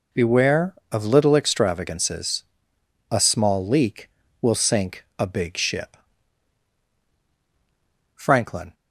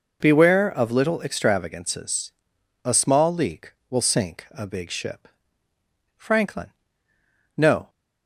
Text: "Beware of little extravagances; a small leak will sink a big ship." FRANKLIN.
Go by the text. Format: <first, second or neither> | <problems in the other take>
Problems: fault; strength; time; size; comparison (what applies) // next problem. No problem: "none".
first | goes on to say "No"; slight; from 7.5 s on; 0.32 s long